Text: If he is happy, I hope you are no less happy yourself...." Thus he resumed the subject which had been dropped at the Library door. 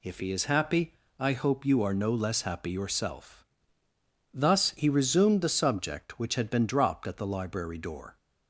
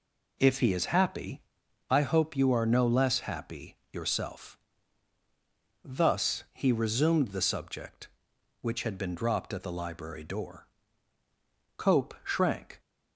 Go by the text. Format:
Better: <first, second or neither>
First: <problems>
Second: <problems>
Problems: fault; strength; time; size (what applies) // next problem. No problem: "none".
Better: first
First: none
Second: pauses between "happy" and "yourself"; slight; at 3.7 s; 0.16 s long // goes on to say "Cope shrank"; noticeable; from 11.7 s on; 1.0 s long